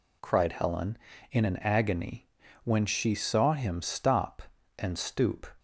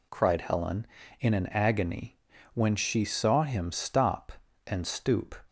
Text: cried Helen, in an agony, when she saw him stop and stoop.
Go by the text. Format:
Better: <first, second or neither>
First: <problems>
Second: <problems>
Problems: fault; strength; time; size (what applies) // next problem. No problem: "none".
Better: neither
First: none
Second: none